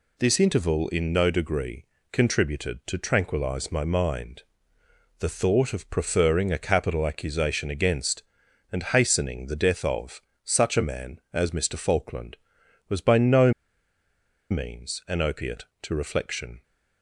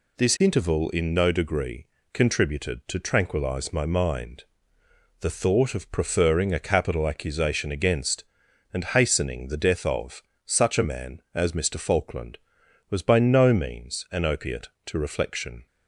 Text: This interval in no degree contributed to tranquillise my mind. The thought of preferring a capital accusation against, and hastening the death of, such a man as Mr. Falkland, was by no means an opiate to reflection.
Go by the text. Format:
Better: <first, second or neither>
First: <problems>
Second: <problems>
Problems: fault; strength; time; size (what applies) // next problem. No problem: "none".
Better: second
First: pauses between "degree" and "contributed"; slight; at 1.8 s; 0.28 s long // pauses between "no" and "means"; at 13.5 s; 0.99 s long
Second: pauses between "degree" and "contributed"; slight; at 1.8 s; 0.28 s long